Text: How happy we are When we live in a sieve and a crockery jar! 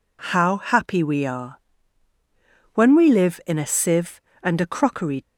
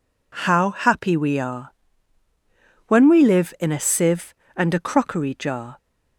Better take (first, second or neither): second